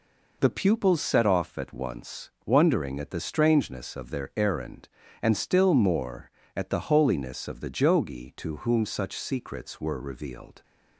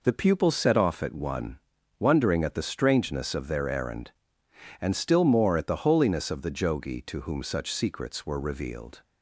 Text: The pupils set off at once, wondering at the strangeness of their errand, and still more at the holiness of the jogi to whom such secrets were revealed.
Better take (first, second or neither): first